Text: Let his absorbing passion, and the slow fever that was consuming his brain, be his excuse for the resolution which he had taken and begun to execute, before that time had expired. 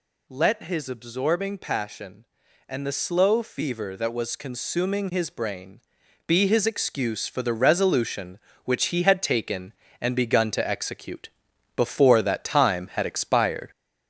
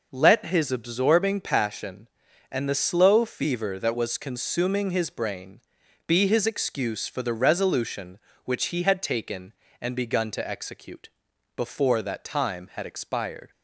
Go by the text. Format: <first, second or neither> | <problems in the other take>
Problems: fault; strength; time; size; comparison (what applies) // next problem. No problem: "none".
second | gets louder; throughout; 4 dB